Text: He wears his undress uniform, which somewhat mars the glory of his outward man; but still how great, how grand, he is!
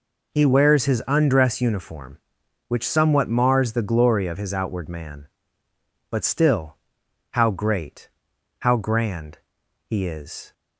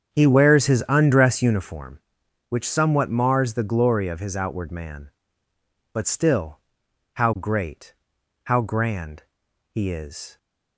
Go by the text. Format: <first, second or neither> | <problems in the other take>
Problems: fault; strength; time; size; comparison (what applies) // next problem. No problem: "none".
first | starts louder than the rest; strong; until 1.9 s; 8 dB // pauses between "still" and "how"; noticeable; at 6.5 s; 0.54 s long; noticeable in the first